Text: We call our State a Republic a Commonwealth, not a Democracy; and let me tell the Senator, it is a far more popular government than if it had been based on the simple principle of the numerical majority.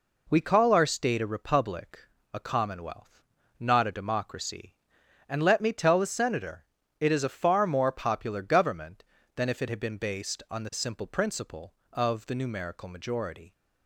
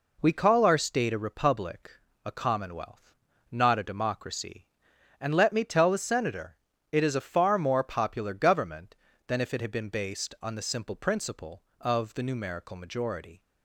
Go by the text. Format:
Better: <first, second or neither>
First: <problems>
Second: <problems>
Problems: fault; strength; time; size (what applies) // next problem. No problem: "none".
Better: neither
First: pauses between "Republic" and "a"; slight; at 1.9 s; 0.34 s long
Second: pauses between "Republic" and "a"; slight; at 1.9 s; 0.34 s long